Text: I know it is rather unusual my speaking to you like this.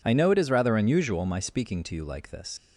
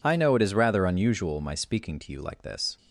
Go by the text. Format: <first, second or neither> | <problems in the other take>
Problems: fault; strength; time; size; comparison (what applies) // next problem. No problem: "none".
second | leaves "this" unfinished; at 2.5 s; 70 ms